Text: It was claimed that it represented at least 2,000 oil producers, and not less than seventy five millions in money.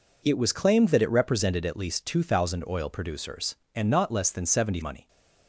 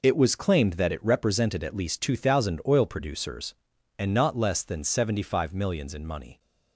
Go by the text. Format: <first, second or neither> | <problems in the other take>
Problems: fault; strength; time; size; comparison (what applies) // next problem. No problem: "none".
second | skips "five millions in"; at 4.7 s